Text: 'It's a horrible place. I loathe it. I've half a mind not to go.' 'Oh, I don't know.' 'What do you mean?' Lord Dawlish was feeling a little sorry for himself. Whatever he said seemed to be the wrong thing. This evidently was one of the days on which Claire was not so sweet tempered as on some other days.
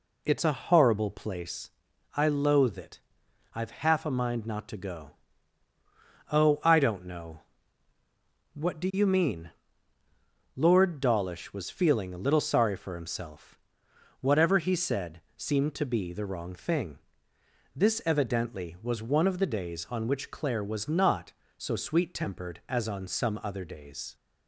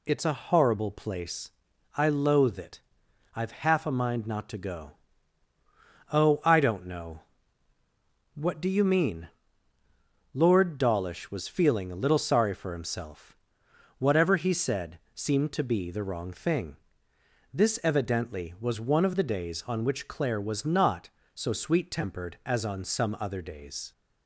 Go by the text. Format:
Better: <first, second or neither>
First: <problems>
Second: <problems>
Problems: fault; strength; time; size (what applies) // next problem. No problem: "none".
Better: second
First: starts louder than the rest; slight; until 1.3 s; 2.5 dB // pauses between "said" and "seemed"; slight; at 15.2 s; 0.16 s long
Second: pauses between "said" and "seemed"; slight; at 14.9 s; 0.16 s long